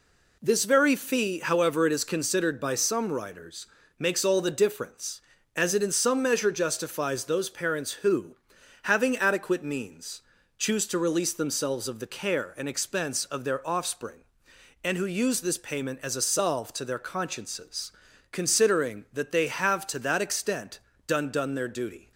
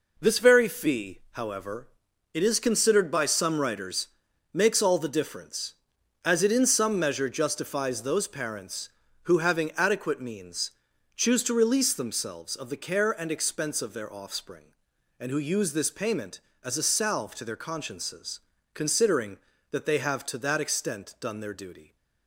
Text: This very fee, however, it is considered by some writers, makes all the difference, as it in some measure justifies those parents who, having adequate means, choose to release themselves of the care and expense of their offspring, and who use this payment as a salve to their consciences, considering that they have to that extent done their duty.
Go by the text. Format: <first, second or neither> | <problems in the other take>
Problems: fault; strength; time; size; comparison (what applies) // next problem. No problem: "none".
second | pauses between "extent" and "done"; slight; at 20.7 s; 0.30 s long // says "done" twice; at 21.3 s